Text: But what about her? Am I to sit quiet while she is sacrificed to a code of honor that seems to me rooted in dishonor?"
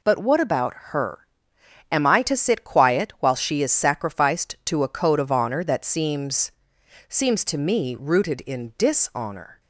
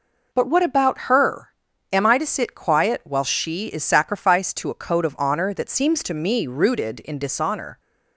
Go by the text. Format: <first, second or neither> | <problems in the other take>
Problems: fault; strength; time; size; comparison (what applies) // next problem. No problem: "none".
second | says "seems" twice; at 7.0 s